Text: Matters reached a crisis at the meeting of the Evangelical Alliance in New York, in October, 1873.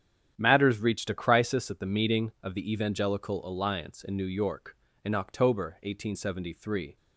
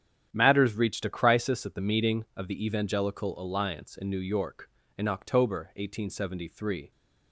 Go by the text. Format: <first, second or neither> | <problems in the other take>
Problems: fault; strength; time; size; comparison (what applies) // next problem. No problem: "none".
neither | starts louder than the rest; strong; the same in both